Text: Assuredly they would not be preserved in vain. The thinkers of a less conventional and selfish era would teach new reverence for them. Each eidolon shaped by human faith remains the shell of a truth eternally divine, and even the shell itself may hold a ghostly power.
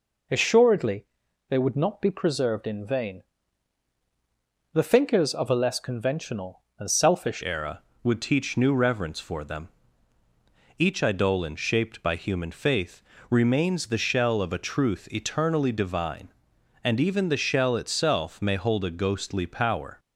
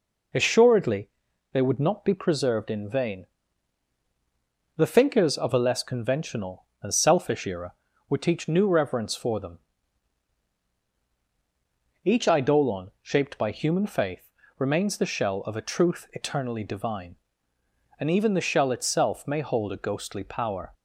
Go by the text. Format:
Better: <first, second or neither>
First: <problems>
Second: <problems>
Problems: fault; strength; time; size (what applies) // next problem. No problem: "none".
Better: second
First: pauses between "Assuredly" and "they"; at 1.0 s; 0.44 s long // changes voice at "era"; from 7.4 s on; 12.5 s long // pauses between "faith" and "remains"; slight; at 13.0 s; 0.28 s long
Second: pauses between "Assuredly" and "they"; at 1.0 s; 0.44 s long // pauses between "faith" and "remains"; slight; at 14.2 s; 0.28 s long